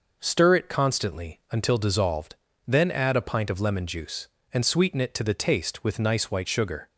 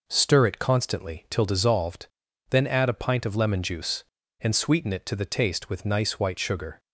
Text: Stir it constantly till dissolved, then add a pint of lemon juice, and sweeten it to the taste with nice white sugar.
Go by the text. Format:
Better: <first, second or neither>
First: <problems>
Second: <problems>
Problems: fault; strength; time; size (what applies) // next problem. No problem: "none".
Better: second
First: says "until" for "till"; at 1.5 s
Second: none